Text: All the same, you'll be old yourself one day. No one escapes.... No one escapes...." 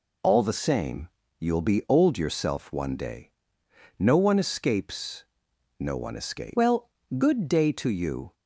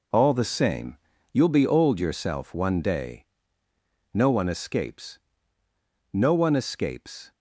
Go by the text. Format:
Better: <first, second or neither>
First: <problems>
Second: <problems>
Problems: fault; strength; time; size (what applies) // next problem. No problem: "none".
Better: second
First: goes on to say "Well good day to you"; strong; from 6.5 s on; 1.7 s long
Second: none